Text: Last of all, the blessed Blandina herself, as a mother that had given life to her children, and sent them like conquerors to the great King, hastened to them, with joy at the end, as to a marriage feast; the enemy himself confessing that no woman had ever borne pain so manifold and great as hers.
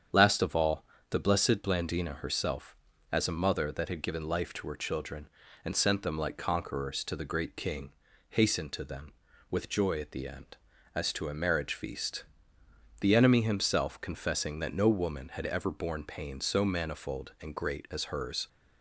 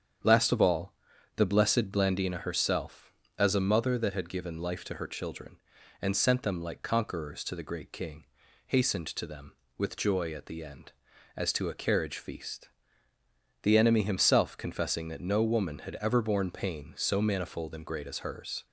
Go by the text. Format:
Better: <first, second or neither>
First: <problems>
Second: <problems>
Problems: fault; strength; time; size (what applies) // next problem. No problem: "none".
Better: first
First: starts louder than the rest; strong; until 1.3 s; 8 dB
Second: starts louder than the rest; strong; until 1.6 s; 8 dB // says "carriage" for "marriage"; at 11.7 s